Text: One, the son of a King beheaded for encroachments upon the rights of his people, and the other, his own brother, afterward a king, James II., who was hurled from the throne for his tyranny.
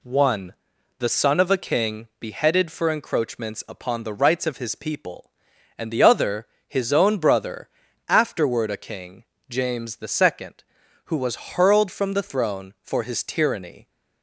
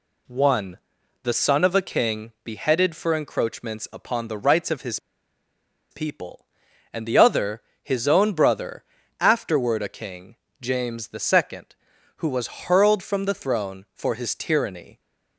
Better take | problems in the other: first | pauses between "his" and "people"; noticeable; at 4.9 s; 0.93 s long

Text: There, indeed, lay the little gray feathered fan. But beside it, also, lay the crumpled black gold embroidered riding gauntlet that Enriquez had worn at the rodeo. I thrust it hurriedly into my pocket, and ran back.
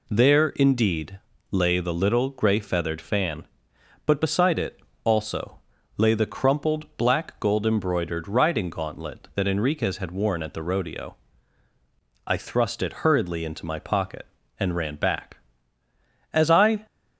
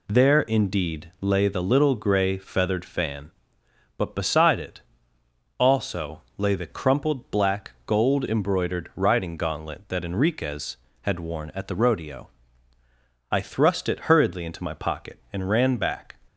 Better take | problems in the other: second | goes on to say "As I"; from 16.3 s on; 0.54 s long

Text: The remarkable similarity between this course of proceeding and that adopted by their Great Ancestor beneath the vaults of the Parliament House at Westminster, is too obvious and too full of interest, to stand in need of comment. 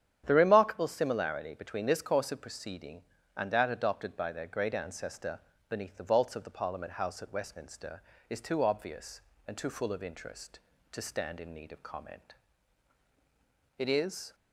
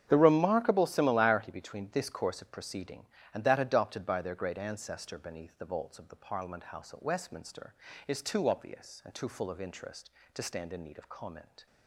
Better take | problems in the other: second | starts louder than the rest; strong; until 1.2 s; 9.5 dB; strong in the second // pauses between "Ancestor" and "beneath"; slight; at 5.3 s; 0.30 s long // goes on to say "It is"; from 13.7 s on; 0.58 s long

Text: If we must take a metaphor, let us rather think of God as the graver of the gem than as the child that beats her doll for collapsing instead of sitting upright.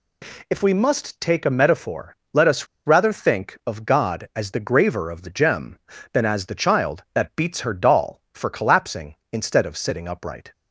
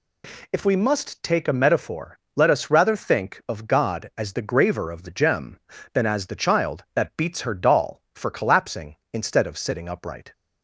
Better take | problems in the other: second | pauses between "us" and "rather"; slight; at 2.6 s; 0.21 s long

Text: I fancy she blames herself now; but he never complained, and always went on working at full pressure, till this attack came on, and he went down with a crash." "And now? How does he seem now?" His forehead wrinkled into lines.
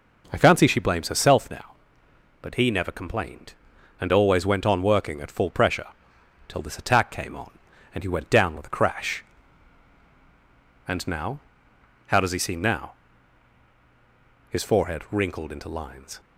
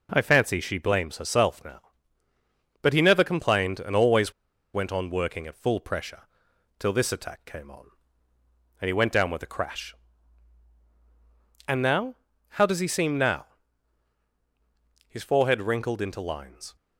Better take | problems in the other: first | pauses between "always" and "went"; at 4.3 s; 0.41 s long

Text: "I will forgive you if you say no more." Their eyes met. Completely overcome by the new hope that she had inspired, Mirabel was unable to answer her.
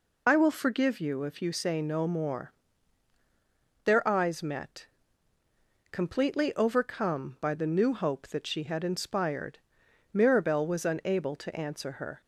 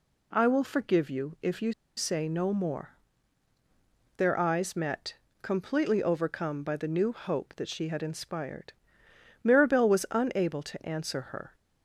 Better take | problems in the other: first | pauses between "you" and "say"; slight; at 1.7 s; 0.23 s long

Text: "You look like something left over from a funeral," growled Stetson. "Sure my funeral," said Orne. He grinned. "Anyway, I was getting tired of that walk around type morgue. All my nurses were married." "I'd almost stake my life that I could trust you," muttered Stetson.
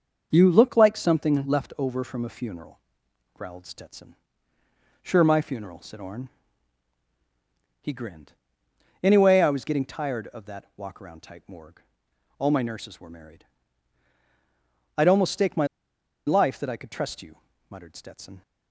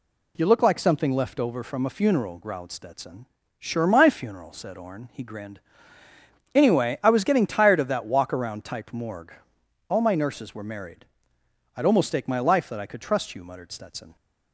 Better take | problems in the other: second | starts louder than the rest; until 1.3 s; 6 dB // pauses between "my" and "life"; noticeable; at 15.6 s; 0.60 s long

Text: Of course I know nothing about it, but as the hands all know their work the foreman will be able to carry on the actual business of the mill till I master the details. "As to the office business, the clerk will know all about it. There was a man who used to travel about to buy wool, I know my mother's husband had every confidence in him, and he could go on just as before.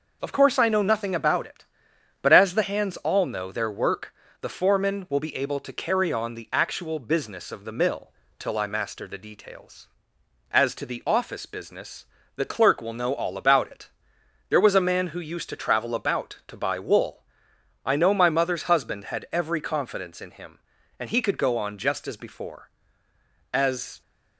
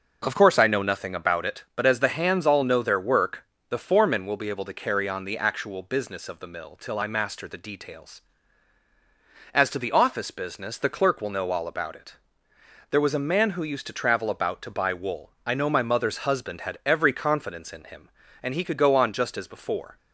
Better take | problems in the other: second | pauses between "work" and "the"; slight; at 4.1 s; 0.28 s long; slight in the second // pauses between "mill" and "till"; slight; at 8.1 s; 0.26 s long // goes on to say "As"; slight; from 23.5 s on; 0.48 s long

